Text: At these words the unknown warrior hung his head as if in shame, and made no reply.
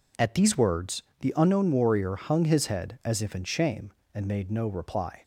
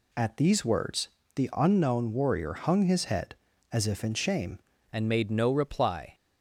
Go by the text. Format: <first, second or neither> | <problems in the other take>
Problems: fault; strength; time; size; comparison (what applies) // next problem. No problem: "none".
first | pauses between "words" and "the"; slight; at 1.0 s; 0.28 s long; slight in the first // changes voice at "and"; from 4.9 s on; 1.2 s long